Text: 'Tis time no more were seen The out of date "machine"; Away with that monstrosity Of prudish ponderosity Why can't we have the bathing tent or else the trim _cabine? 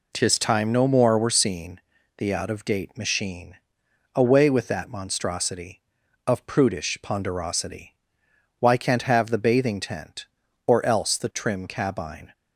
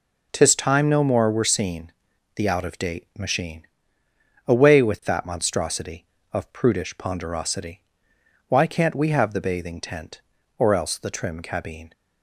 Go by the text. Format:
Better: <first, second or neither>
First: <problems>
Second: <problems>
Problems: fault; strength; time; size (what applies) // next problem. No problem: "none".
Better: second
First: pauses between "seen" and "The"; at 1.8 s; 0.38 s long // pauses between "ponderosity" and "Why"; noticeable; at 7.9 s; 0.62 s long // skips "we"; at 9.0 s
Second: pauses between "seen" and "The"; at 1.9 s; 0.44 s long // pauses between "ponderosity" and "Why"; noticeable; at 7.8 s; 0.66 s long